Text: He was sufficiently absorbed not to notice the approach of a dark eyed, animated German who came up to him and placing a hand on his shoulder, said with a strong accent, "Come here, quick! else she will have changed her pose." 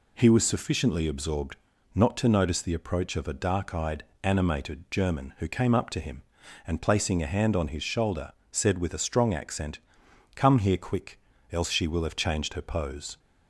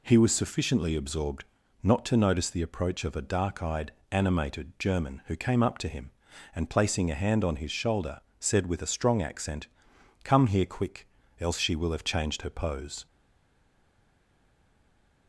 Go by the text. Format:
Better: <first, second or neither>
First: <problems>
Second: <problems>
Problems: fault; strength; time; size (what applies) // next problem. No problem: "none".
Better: first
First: pauses between "absorbed" and "not"; at 1.5 s; 0.38 s long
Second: pauses between "absorbed" and "not"; at 1.4 s; 0.38 s long // stays silent after the last word; from 13.0 s on; 2.2 s long